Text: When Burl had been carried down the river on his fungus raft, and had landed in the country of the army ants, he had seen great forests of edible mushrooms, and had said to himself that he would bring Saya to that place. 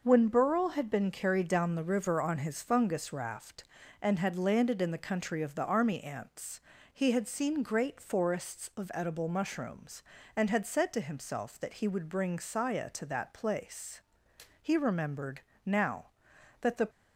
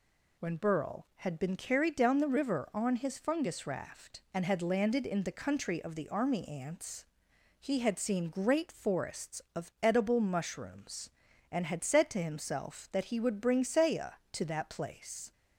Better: second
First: goes on to say "He remembered now that the"; strong; from 14.6 s on; 2.2 s long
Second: none

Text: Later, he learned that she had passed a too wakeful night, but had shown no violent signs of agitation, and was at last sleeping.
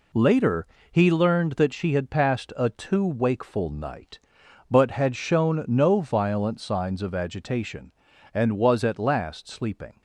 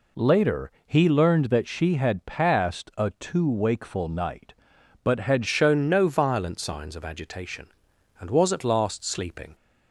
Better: first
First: none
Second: changes voice at "shown"; from 5.4 s on; 4.1 s long

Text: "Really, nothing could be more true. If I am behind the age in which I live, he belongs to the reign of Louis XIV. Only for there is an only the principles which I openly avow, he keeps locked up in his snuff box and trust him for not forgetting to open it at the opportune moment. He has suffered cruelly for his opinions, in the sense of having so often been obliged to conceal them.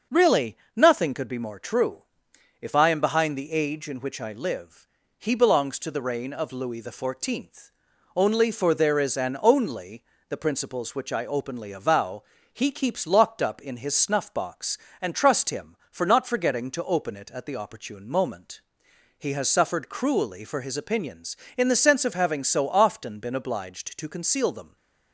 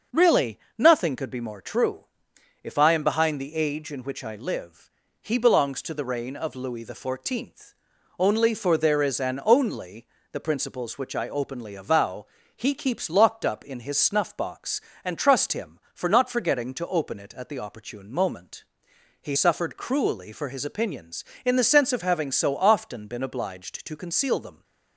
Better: first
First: pauses between "only" and "the"; slight; at 10.0 s; 0.26 s long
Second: pauses between "only" and "the"; slight; at 10.0 s; 0.26 s long // skips "has"; at 19.3 s

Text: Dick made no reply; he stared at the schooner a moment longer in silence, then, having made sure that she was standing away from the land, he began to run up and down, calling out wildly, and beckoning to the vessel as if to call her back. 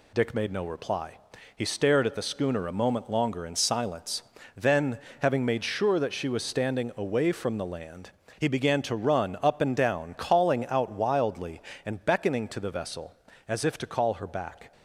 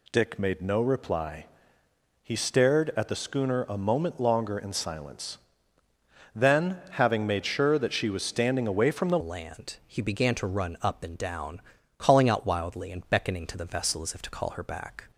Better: first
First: none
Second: changes voice at "land"; from 9.2 s on; 5.9 s long

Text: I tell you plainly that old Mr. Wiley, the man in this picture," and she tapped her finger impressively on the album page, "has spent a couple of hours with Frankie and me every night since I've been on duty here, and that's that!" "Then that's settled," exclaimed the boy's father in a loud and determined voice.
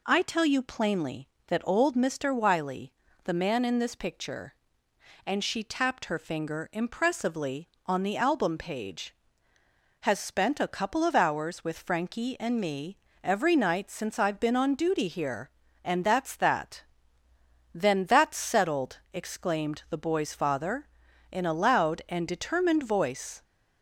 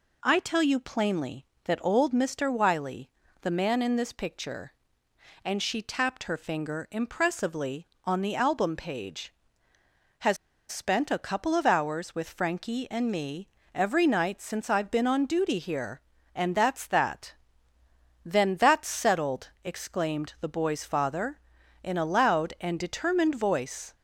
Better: first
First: pauses between "me" and "every"; slight; at 12.9 s; 0.24 s long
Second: pauses between "has" and "spent"; slight; at 10.3 s; 0.32 s long // pauses between "me" and "every"; slight; at 13.4 s; 0.24 s long

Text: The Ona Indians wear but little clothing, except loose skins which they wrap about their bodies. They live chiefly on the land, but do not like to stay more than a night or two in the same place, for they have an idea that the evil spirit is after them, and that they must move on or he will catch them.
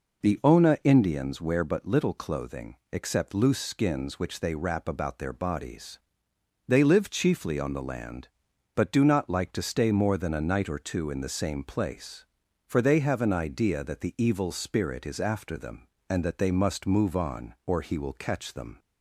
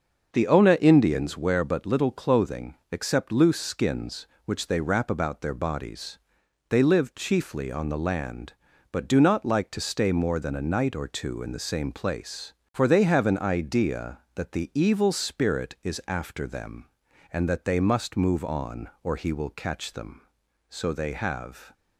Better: first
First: none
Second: starts louder than the rest; until 1.3 s; 6.5 dB // goes on to say "So they have"; noticeable; from 20.6 s on; 1.0 s long

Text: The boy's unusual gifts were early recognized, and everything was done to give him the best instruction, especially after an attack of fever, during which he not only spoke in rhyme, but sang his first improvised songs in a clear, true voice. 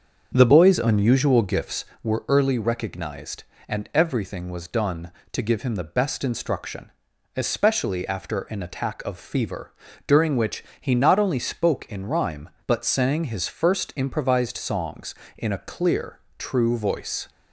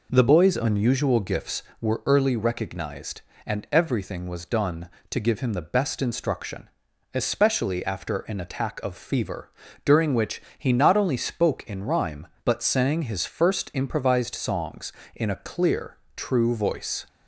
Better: second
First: starts louder than the rest; until 1.8 s; 7 dB // pauses between "which" and "he"; slight; at 10.6 s; 0.18 s long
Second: pauses between "which" and "he"; slight; at 10.4 s; 0.18 s long

